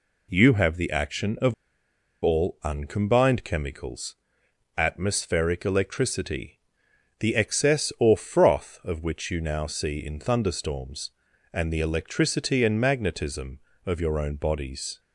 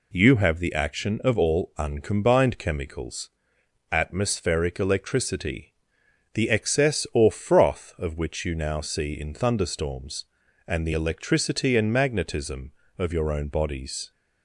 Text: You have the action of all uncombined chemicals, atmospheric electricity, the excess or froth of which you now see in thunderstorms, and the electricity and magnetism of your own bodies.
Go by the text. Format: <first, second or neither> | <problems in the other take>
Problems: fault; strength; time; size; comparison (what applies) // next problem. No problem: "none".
second | pauses between "of" and "all"; noticeable; at 1.5 s; 0.69 s long